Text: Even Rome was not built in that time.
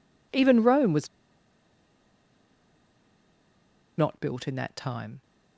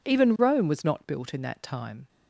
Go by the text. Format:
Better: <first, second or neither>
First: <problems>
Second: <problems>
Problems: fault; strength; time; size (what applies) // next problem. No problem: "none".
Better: second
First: pauses between "was" and "not"; strong; at 1.0 s; 2.8 s long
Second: none